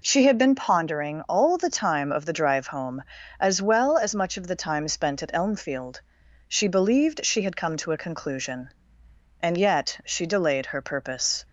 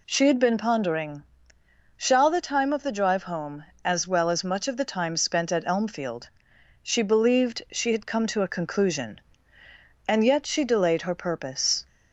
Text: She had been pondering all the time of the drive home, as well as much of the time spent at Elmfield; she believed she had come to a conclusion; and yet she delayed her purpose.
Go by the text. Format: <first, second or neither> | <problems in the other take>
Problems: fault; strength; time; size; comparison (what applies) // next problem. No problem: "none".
first | says "shall" for "all"; at 1.9 s